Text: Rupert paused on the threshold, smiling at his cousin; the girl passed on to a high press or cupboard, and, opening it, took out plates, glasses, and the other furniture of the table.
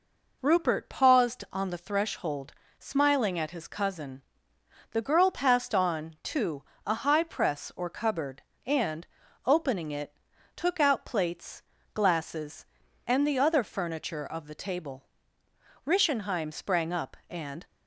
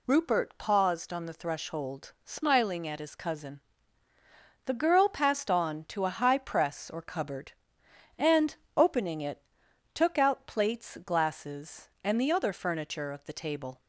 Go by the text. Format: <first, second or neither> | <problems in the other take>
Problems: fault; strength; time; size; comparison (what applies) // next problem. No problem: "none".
second | pauses between "to" and "a"; slight; at 6.6 s; 0.24 s long // goes on to say "Rischenheim sprang up and"; strong; from 15.8 s on; 1.8 s long